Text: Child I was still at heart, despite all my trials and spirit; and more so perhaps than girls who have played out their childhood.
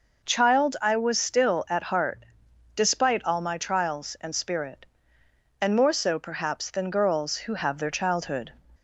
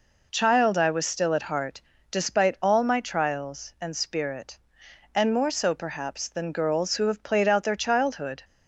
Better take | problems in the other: second | skips "played out"; at 7.7 s

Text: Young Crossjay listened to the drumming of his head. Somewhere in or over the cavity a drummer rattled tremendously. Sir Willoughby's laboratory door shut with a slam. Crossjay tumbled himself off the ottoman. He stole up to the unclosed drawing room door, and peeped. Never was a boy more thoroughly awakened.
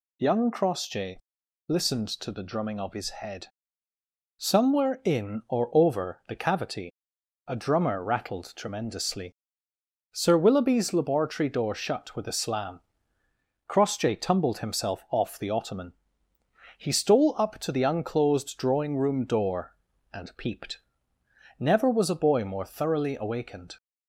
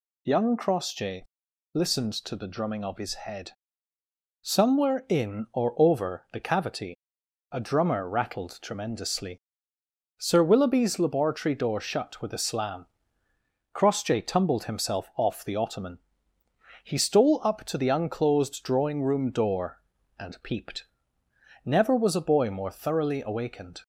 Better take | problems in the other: neither | pauses between "Crossjay" and "listened"; noticeable; the same in both // pauses between "cavity" and "a"; noticeable; the same in both

